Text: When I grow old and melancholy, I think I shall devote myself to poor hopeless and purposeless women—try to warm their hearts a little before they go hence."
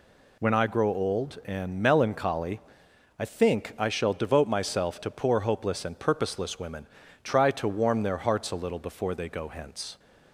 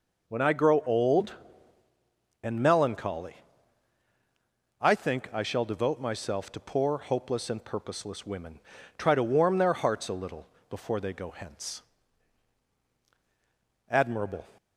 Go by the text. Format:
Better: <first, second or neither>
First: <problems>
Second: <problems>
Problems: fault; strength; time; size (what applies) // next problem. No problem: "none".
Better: first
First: none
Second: pauses between "little" and "before"; slight; at 10.4 s; 0.24 s long // goes on to say "Admirable"; from 13.8 s on; 0.58 s long